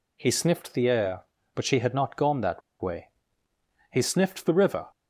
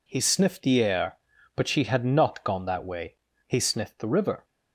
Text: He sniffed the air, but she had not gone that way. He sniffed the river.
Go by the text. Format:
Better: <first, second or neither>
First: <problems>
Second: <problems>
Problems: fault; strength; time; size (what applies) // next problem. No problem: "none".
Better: second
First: pauses between "that" and "way"; slight; at 2.6 s; 0.21 s long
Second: none